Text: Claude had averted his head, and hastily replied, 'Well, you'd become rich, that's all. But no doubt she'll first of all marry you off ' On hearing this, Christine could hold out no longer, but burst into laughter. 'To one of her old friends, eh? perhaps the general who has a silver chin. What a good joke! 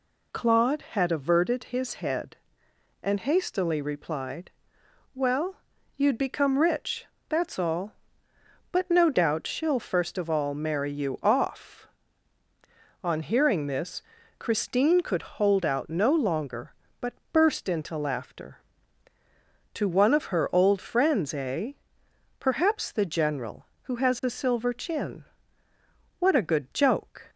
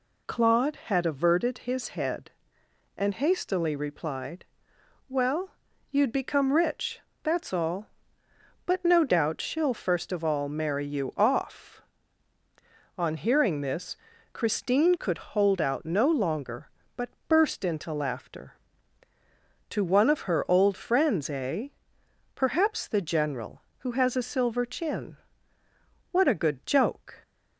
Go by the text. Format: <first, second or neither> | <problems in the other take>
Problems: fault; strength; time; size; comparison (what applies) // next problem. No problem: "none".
neither | pauses between "but" and "burst"; slight; the same in both